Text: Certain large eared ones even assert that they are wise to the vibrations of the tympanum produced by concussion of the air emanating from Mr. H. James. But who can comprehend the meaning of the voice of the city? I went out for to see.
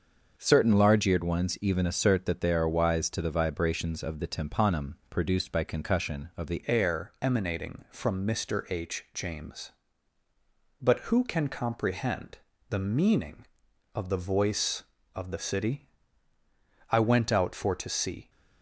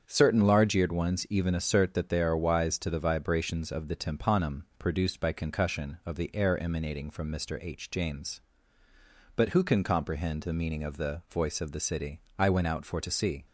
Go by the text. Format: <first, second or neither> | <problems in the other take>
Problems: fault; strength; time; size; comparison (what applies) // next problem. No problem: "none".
second | starts louder than the rest; until 1.3 s; 6.5 dB; strong in the second // changes voice at "air"; from 6.6 s on; 11.6 s long // pauses between "comprehend" and "the"; slight; at 12.3 s; 0.32 s long